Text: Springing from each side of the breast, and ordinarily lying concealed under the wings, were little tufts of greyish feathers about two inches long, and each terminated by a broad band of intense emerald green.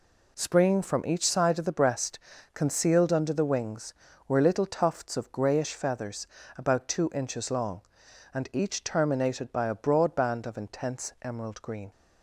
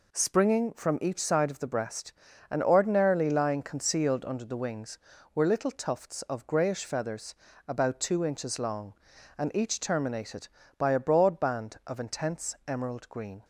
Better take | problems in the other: second | skips "and ordinarily lying"; at 2.3 s // pauses between "feathers" and "about"; slight; at 6.2 s; 0.30 s long; slight in the second

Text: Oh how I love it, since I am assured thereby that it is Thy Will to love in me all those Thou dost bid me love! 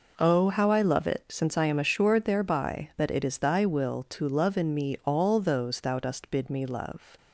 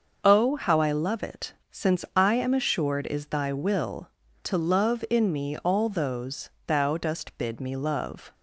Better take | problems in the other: first | starts louder than the rest; until 1.2 s; 6.5 dB // skips "thereby that it"; at 3.0 s // pauses between "those" and "Thou"; slight; at 6.4 s; 0.18 s long

